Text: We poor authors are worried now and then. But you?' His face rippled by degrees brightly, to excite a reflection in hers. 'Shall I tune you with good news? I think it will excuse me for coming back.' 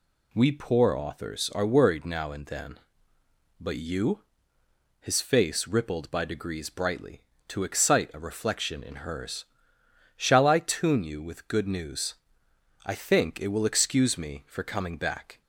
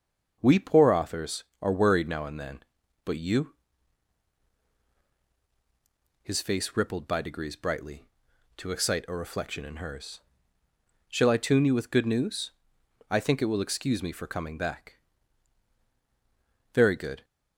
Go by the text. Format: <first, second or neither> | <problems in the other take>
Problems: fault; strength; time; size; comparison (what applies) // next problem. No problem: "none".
first | starts louder than the rest; noticeable; until 1.4 s; 6 dB // goes on to say "Very good"; from 16.7 s on; 0.52 s long